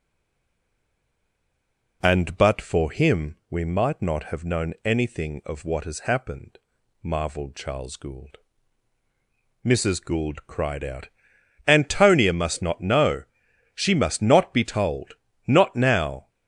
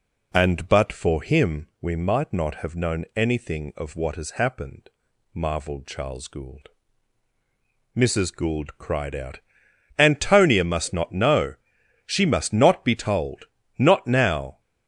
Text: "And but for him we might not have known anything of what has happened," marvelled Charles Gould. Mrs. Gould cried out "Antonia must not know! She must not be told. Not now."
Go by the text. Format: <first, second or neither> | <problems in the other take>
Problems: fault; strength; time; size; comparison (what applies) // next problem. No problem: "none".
second | stays silent before the first word; noticeable; until 2.0 s; 2.0 s long // pauses between "out" and "Antonia"; noticeable; at 11.0 s; 0.58 s long; noticeable in the second